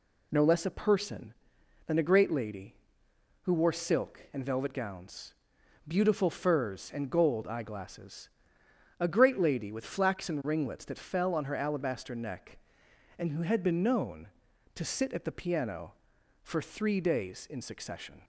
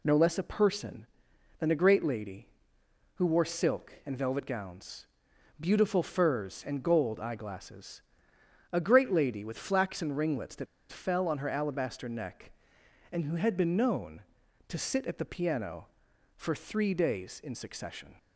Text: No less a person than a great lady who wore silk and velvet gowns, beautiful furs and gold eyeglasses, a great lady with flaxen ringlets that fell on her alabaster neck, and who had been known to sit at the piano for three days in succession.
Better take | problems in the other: first | pauses between "that" and "fell"; slight; at 10.6 s; 0.25 s long

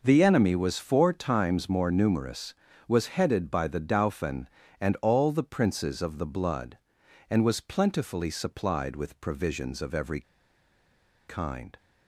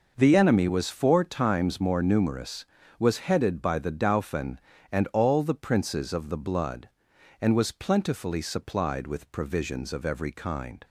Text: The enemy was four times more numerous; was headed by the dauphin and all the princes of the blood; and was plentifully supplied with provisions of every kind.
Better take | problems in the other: second | pauses between "every" and "kind"; at 10.2 s; 1.0 s long

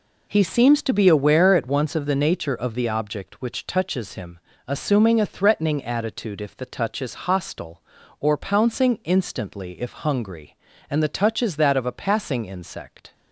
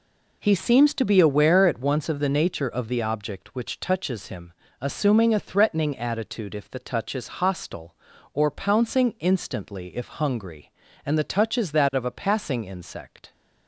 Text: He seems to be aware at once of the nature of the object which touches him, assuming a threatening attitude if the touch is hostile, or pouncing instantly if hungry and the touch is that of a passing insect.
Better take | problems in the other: neither | none

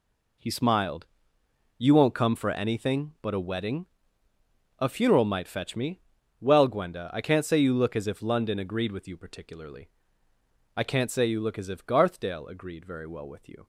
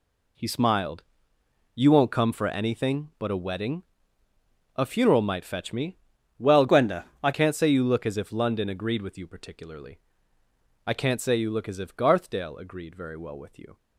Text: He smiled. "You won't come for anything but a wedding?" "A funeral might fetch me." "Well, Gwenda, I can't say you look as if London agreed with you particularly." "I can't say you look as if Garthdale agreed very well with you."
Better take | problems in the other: first | changes voice from "Gwenda" to "I"; from 6.6 to 7.3 s; 0.7 s long

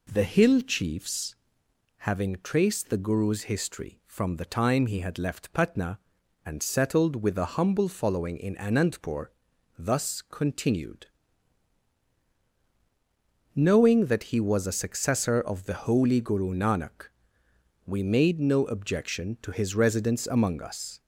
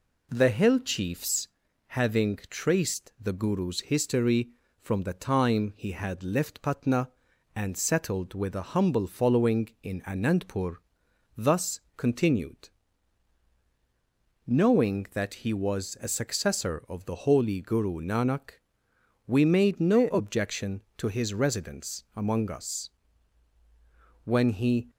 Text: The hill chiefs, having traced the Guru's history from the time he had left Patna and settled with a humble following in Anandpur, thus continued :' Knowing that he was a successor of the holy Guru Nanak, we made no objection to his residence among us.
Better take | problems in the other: first | pauses between "thus" and "continued"; slight; at 11.7 s; 0.16 s long // goes on to say "When he"; noticeable; from 24.2 s on; 0.66 s long

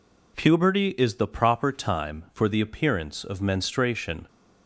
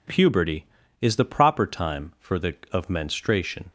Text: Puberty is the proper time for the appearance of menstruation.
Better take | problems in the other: first | skips "appearance"; at 2.6 s

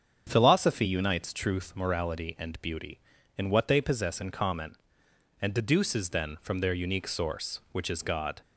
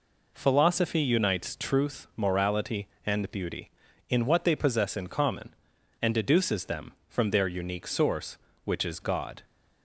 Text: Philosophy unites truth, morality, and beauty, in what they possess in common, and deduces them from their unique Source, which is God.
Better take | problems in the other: second | starts louder than the rest; strong; until 1.2 s; 7.5 dB // says "then" for "them"; at 6.1 s

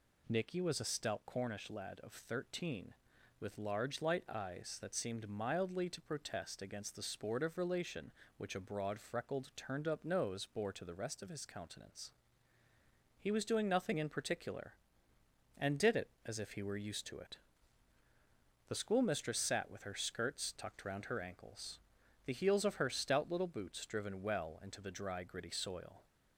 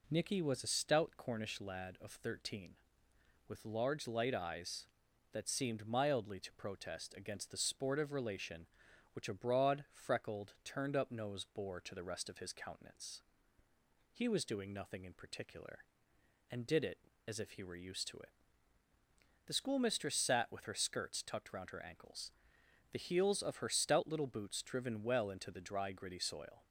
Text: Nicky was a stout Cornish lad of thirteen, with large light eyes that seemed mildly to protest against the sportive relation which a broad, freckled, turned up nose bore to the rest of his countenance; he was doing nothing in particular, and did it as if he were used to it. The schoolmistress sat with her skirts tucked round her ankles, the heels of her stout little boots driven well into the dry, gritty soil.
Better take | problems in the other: neither | none

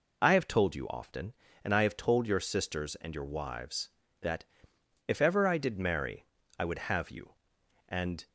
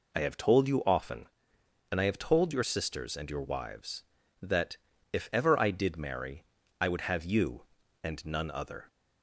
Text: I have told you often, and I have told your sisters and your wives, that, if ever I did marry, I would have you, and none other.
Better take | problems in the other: second | stops before "none other"; at 8.2 s

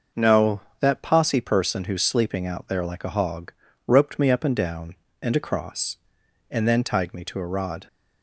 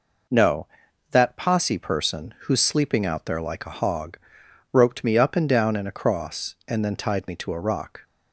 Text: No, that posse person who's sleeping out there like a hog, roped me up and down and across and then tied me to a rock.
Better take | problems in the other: second | says "rod" for "rock"; at 7.4 s

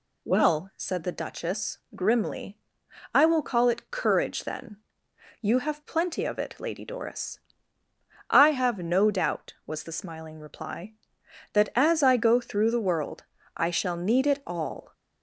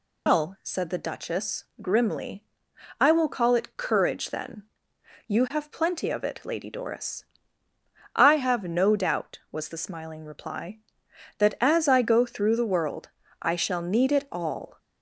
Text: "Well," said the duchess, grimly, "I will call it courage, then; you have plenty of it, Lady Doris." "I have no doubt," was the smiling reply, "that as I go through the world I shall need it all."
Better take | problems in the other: first | loses the start of "Well"; at 0.2 s; 140 ms // pauses between "world" and "I"; slight; at 13.0 s; 0.32 s long; slight in the first

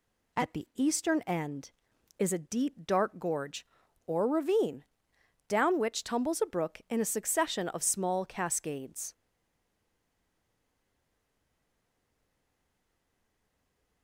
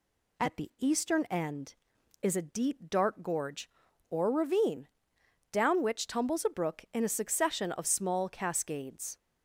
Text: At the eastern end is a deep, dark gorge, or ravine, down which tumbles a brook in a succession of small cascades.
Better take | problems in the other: second | stays silent after the last word; strong; from 9.1 s on; 4.9 s long

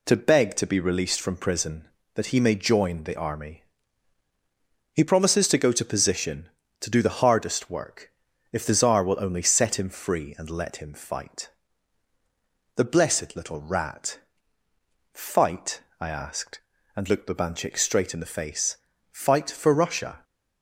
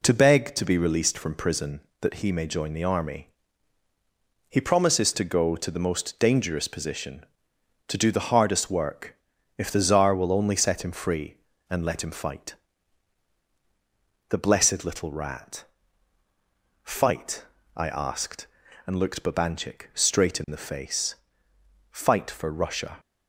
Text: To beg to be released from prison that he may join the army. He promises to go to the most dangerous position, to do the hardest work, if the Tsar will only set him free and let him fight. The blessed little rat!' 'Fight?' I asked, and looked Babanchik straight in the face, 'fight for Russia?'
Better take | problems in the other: second | skips "the most dangerous"; at 5.8 s

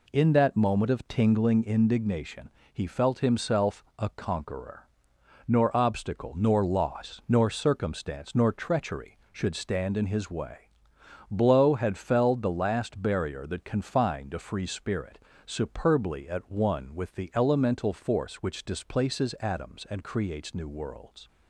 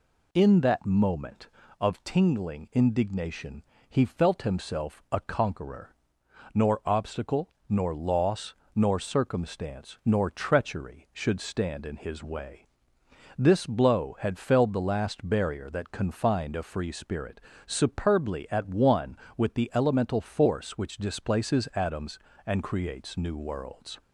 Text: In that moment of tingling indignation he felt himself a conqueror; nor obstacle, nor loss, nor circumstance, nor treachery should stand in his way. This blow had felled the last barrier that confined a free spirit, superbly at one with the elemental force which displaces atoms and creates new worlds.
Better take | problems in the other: second | pauses between "indignation" and "he"; slight; at 2.4 s; 0.24 s long; slight in the second // pauses between "himself" and "a"; slight; at 3.8 s; 0.16 s long // skips "This"; at 10.9 s

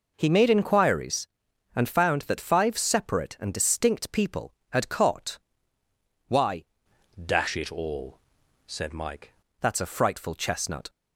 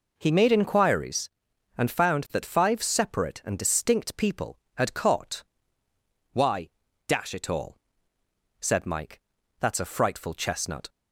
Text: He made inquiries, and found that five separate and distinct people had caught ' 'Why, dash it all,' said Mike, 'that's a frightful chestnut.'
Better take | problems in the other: second | changes voice from "dash" to "Mike"; from 7.2 to 9.3 s; 2.1 s long

